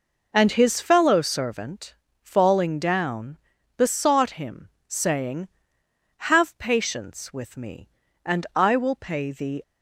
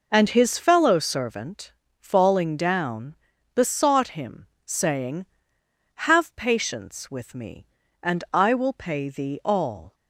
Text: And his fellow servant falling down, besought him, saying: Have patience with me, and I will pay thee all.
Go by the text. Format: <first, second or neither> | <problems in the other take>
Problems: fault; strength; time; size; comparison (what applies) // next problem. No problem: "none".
second | pauses between "servant" and "falling"; slight; at 1.9 s; 0.28 s long; slight in the second // stops before "all"; at 9.6 s